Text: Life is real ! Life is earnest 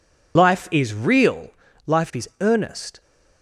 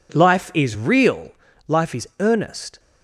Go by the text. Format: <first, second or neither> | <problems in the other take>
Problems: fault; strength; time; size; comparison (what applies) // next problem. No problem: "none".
second | loses the start of "Life"; at 0.3 s; 85 ms